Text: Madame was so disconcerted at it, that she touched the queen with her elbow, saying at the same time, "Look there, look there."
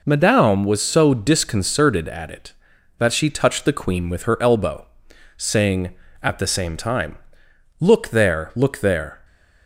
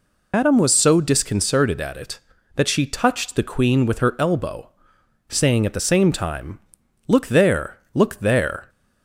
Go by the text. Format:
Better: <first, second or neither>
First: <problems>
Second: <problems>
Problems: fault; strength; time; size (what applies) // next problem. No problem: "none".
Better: first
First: none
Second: loses the start of "Madame"; at 0.3 s; 115 ms